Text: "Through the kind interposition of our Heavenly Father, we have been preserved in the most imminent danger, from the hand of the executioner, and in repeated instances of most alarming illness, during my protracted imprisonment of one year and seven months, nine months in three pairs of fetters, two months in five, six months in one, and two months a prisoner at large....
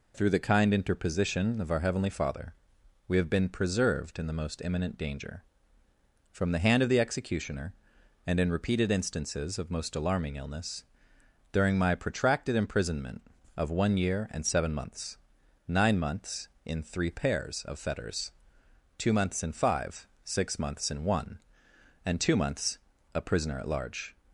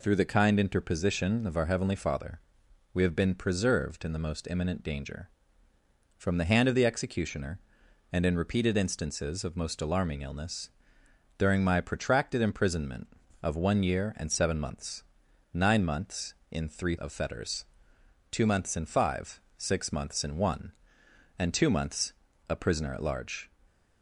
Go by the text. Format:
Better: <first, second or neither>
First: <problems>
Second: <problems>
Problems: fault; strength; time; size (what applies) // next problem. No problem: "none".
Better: first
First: pauses between "months" and "a"; at 22.7 s; 0.38 s long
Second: skips "pairs"; at 16.9 s // pauses between "months" and "a"; at 22.1 s; 0.38 s long // stays silent after the last word; slight; from 23.4 s on; 0.6 s long